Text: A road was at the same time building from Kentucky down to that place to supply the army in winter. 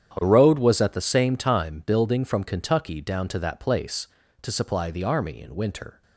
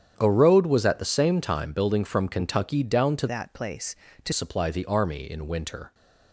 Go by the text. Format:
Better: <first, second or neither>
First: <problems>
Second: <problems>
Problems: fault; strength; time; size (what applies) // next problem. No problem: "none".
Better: first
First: starts louder than the rest; strong; until 1.1 s; 9 dB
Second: starts louder than the rest; strong; until 1.1 s; 9 dB // changes voice from "that" to "to"; from 3.2 to 4.3 s; 1.1 s long